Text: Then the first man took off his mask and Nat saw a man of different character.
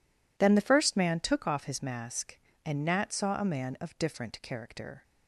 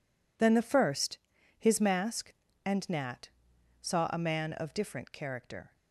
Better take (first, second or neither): first